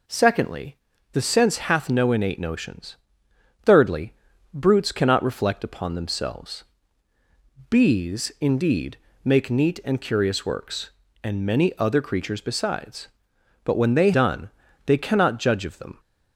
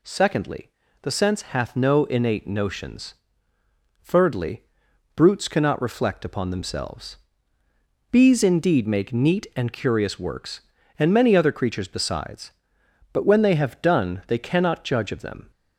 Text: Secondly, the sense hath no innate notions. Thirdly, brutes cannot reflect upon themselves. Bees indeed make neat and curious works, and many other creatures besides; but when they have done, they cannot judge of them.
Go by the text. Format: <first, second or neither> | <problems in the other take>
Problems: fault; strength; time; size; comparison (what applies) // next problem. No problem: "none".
second | pauses between "indeed" and "make"; slight; at 8.9 s; 0.26 s long // skips "have"; at 14.1 s